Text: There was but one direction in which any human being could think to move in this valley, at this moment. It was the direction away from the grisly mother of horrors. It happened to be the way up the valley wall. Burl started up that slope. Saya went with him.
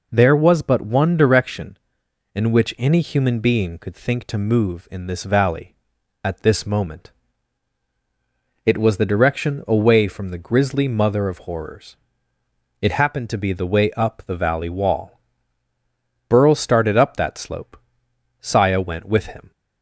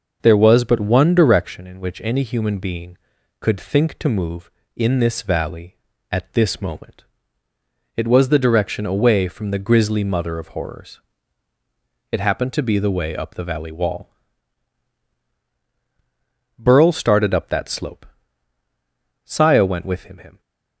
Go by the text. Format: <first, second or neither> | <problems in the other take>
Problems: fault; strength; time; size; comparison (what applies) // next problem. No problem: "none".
first | starts louder than the rest; noticeable; until 1.2 s; 6 dB // says "him" twice; at 20.1 s